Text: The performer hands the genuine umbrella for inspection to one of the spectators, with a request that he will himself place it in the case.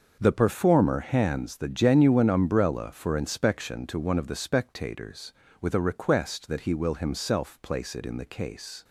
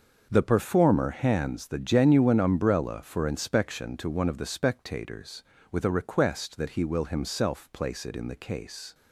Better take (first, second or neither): neither